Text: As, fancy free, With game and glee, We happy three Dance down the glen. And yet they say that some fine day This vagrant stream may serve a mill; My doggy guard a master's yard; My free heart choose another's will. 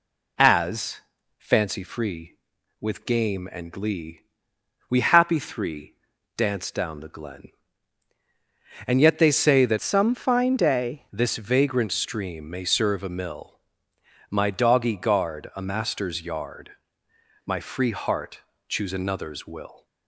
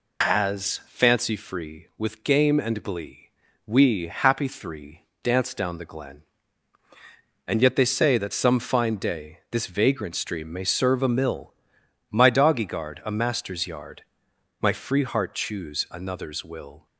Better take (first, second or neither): second